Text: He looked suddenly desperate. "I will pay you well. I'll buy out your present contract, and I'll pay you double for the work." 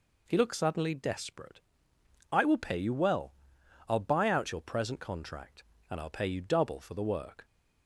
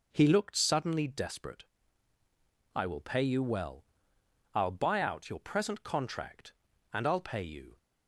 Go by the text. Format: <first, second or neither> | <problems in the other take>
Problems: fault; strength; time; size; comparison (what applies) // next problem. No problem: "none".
first | stops before "double for the work"; at 7.7 s